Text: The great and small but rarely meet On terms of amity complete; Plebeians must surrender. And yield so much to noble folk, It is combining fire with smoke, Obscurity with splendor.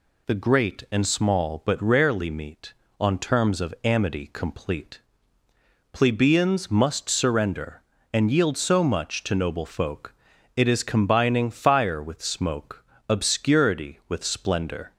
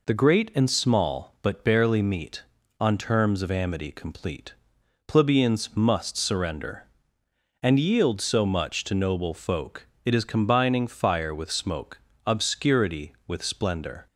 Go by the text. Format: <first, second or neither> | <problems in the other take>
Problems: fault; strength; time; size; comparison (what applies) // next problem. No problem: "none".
first | says "barely" for "rarely"; at 1.6 s